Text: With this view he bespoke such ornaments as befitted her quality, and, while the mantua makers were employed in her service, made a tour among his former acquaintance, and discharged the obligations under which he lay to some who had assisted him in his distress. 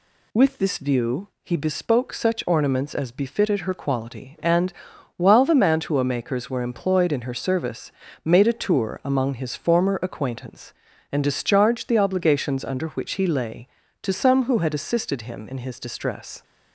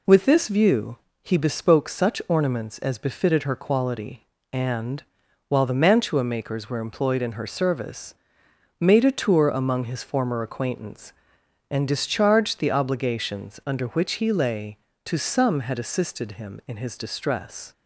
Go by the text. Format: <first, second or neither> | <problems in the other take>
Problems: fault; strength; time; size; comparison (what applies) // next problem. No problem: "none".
first | pauses between "view" and "he"; slight; at 0.9 s; 0.26 s long // skips "who"; at 15.6 s